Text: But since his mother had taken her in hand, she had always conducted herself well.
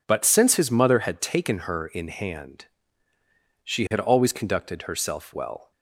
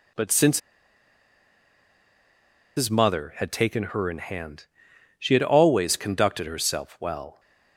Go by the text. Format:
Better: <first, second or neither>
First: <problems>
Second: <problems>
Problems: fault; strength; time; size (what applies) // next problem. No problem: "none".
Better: first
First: none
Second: pauses between "since" and "his"; strong; at 0.5 s; 2.1 s long